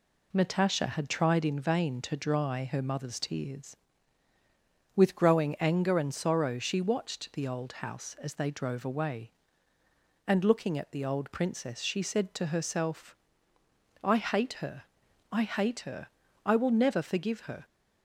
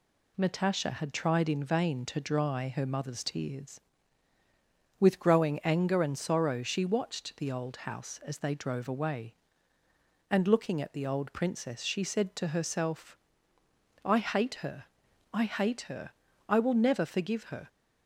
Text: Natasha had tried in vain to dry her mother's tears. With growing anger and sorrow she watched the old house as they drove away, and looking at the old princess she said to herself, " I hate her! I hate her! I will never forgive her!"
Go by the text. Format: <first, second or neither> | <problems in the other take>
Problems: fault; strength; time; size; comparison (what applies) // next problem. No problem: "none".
second | starts louder than the rest; slight; until 1.4 s; 2 dB